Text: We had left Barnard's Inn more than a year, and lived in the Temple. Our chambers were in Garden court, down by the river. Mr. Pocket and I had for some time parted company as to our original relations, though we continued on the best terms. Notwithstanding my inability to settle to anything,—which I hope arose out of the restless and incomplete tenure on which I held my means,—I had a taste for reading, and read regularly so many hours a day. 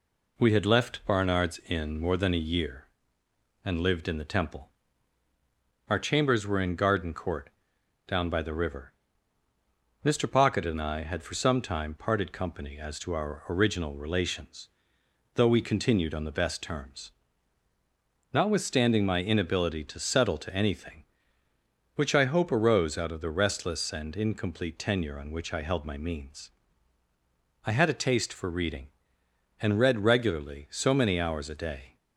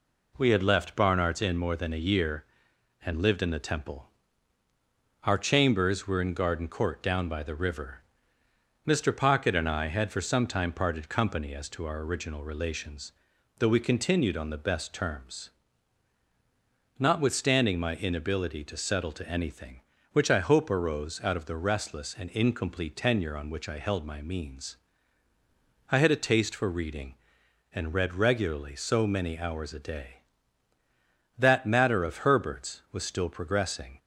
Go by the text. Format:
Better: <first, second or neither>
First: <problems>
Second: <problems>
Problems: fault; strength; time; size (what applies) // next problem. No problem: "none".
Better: first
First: none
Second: goes on to say "That matter of Herbert's was still progressing"; strong; from 31.3 s on; 2.6 s long